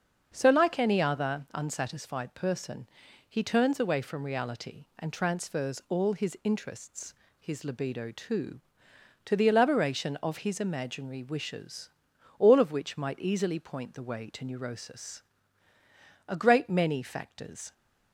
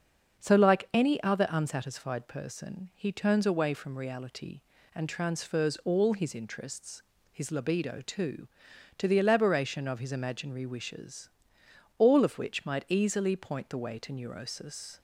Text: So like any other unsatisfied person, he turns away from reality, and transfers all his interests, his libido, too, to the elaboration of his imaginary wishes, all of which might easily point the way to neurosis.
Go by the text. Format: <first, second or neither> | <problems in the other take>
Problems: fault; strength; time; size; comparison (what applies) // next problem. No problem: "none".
second | starts louder than the rest; until 1.3 s; 6.5 dB; also in the second // goes on to say "A great many factors"; from 16.2 s on; 1.4 s long